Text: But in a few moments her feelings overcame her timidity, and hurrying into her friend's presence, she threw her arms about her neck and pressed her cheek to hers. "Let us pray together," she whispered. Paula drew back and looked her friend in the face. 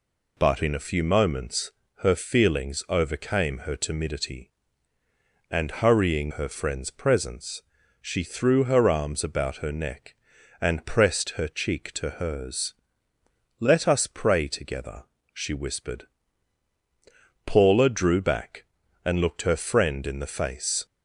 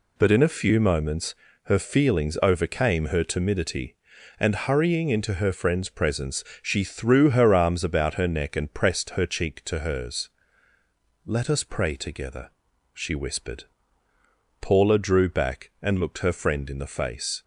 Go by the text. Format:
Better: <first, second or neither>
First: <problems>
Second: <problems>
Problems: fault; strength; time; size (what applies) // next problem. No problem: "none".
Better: second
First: pauses between "moments" and "her"; slight; at 1.7 s; 0.30 s long // skips "into"; at 6.3 s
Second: pauses between "moments" and "her"; slight; at 1.3 s; 0.30 s long